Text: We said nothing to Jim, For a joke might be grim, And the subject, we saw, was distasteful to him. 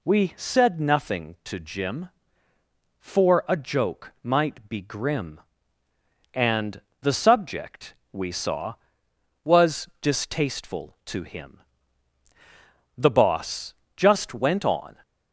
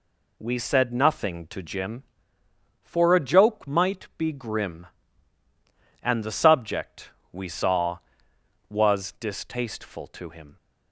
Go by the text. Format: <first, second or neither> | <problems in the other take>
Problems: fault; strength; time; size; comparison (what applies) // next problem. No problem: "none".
second | pauses between "And" and "the"; slight; at 6.7 s; 0.22 s long // goes on to say "The Boss just went on"; strong; from 12.9 s on; 2.0 s long